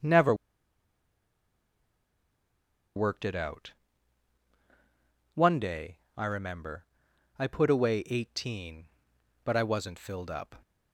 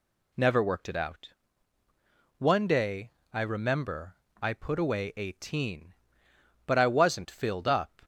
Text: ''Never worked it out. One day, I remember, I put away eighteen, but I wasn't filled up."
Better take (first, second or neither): second